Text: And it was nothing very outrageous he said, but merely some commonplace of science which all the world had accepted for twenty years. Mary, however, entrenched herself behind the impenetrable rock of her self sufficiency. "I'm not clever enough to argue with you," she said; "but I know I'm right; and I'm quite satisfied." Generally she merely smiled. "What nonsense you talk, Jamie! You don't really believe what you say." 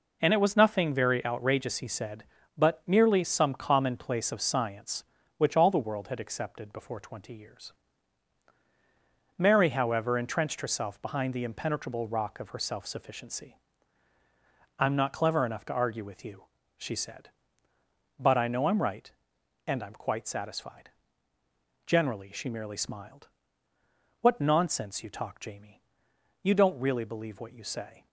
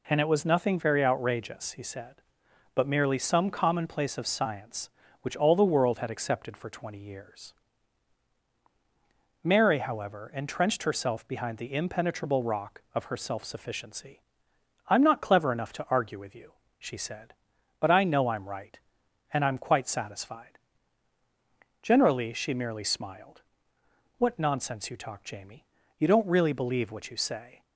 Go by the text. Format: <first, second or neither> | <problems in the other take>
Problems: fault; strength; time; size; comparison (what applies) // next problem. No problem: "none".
second | says "before" for "for"; at 6.7 s